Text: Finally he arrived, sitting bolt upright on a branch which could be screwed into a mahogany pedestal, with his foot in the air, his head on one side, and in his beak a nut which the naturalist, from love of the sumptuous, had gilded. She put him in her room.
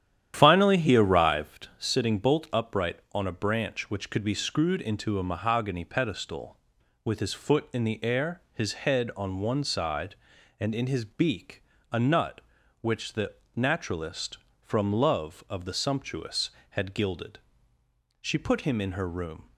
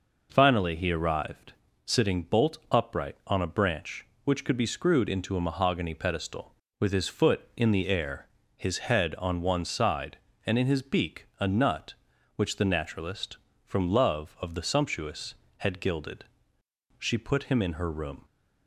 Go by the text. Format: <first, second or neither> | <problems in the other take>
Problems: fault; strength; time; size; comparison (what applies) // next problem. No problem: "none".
second | starts louder than the rest; strong; until 1.7 s; 10.5 dB // pauses between "beak" and "a"; slight; at 11.6 s; 0.26 s long // pauses between "the" and "naturalist"; slight; at 13.3 s; 0.22 s long